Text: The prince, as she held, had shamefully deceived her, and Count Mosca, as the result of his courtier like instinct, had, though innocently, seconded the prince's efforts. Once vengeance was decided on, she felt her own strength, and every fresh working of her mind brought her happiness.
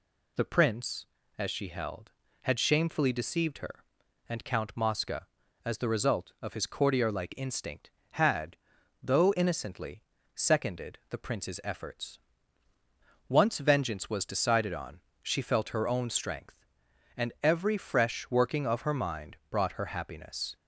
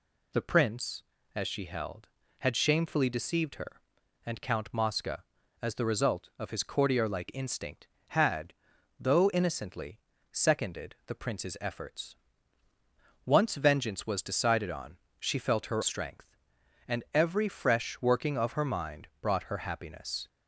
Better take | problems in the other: first | skips "own"; at 15.8 s

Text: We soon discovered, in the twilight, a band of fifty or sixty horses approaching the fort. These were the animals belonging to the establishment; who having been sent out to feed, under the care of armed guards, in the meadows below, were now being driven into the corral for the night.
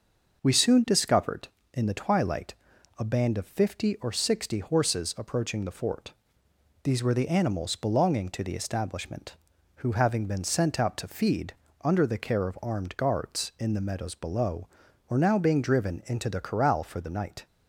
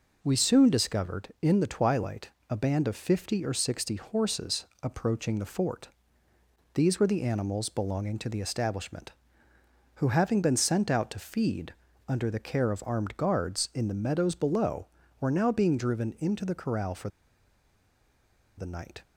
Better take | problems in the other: first | pauses between "horses" and "approaching"; slight; at 4.6 s; 0.16 s long // pauses between "for" and "the"; strong; at 17.0 s; 1.4 s long

